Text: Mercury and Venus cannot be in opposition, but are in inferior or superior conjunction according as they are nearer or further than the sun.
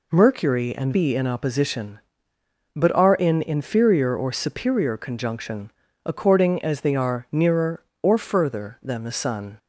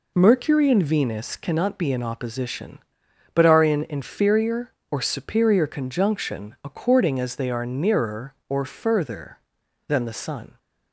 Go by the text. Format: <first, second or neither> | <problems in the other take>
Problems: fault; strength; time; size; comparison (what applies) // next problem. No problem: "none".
second | skips "Venus cannot"; at 0.9 s // pauses between "conjunction" and "according"; slight; at 5.6 s; 0.36 s long